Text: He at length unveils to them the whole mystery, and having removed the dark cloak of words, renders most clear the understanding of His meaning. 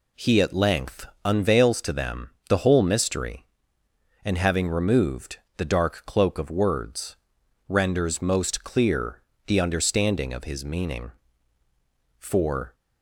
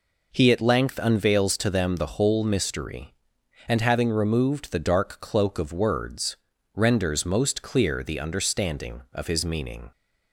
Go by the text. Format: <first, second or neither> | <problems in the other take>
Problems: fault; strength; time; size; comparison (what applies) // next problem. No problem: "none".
second | pauses between "length" and "unveils"; slight; at 1.0 s; 0.18 s long // pauses between "them" and "the"; slight; at 2.2 s; 0.18 s long // pauses between "removed" and "the"; slight; at 5.3 s; 0.18 s long // pauses between "clear" and "the"; slight; at 9.2 s; 0.24 s long // goes on to say "For"; from 12.1 s on; 0.56 s long